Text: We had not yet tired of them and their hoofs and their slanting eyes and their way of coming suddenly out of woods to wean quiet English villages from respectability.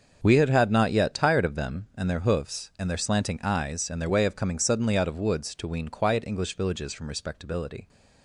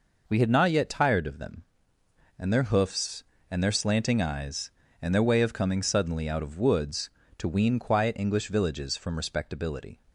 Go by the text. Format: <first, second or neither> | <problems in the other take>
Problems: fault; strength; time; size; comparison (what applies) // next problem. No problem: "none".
second | starts louder than the rest; until 1.2 s; 6.5 dB // says "had" twice; at 0.5 s